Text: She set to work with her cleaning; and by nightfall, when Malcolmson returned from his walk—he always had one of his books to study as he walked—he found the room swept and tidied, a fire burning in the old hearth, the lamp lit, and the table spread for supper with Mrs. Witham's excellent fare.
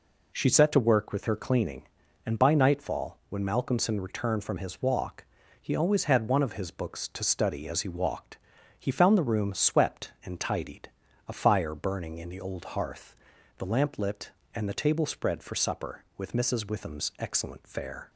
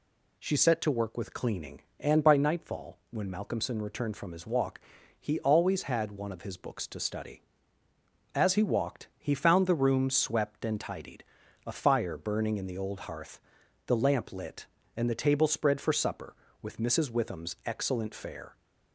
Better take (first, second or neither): first